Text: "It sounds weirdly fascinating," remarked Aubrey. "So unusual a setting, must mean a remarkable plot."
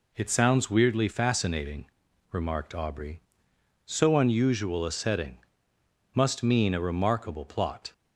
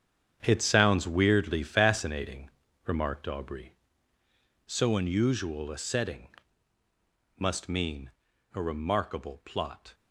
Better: first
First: none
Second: gets quieter; strong; throughout; 11 dB // pauses between "mean" and "a"; noticeable; at 8.0 s; 0.46 s long

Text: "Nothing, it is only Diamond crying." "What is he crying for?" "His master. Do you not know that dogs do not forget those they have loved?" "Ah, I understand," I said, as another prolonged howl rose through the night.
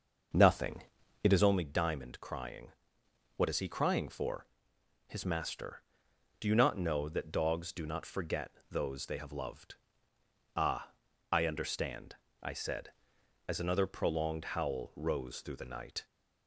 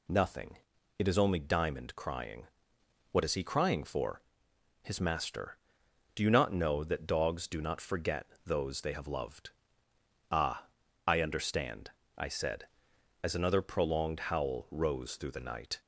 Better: second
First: starts louder than the rest; noticeable; until 1.6 s; 6 dB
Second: none

